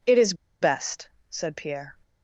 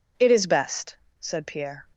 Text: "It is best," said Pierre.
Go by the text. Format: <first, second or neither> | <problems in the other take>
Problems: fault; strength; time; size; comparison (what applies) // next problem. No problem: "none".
second | pauses between "is" and "best"; slight; at 0.3 s; 0.27 s long